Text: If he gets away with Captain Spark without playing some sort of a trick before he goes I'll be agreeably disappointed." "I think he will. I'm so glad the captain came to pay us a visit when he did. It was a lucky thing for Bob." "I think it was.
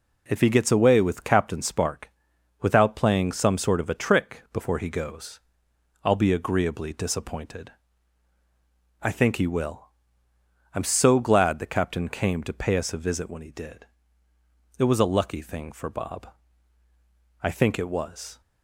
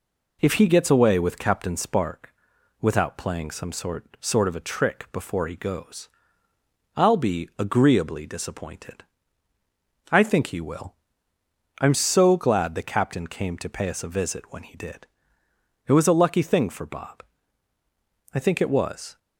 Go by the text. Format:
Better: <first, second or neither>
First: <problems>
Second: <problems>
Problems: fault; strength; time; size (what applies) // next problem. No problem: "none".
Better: first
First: pauses between "Spark" and "without"; noticeable; at 2.1 s; 0.50 s long // pauses between "goes" and "I'll"; noticeable; at 5.3 s; 0.64 s long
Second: pauses between "Spark" and "without"; noticeable; at 2.3 s; 0.48 s long // says "sort" twice; at 4.2 s // pauses between "goes" and "I'll"; noticeable; at 6.0 s; 0.88 s long